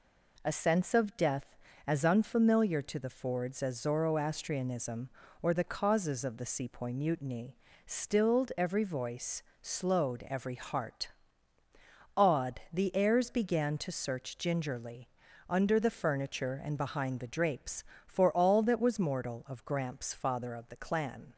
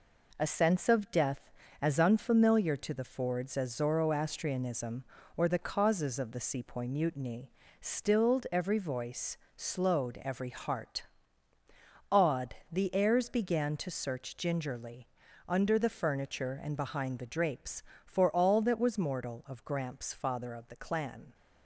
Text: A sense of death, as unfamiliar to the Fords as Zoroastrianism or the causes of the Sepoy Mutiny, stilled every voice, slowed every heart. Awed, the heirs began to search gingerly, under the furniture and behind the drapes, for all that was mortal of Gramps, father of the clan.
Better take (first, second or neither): first